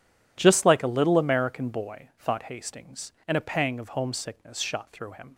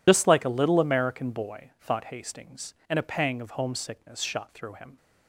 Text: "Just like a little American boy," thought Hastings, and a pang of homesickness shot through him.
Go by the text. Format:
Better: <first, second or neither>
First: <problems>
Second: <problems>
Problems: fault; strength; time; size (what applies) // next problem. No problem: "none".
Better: first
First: none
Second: loses the start of "Just"; at 0.0 s; 85 ms